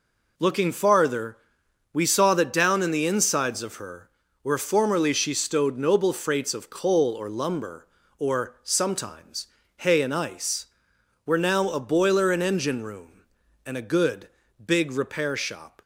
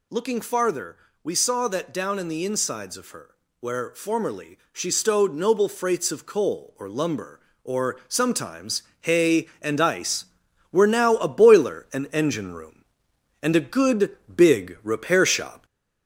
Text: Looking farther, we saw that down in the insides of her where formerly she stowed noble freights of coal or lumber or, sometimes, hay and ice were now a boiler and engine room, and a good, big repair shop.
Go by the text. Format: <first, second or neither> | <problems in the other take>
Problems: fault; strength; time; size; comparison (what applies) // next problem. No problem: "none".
first | gets louder; slight; throughout; 3 dB // pauses between "her" and "where"; slight; at 3.3 s; 0.28 s long; slight in the first